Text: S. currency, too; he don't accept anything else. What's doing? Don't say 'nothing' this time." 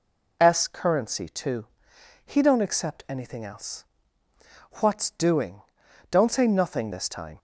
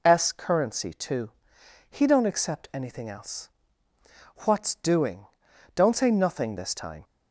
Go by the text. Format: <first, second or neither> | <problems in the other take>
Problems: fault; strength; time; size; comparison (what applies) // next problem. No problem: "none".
neither | none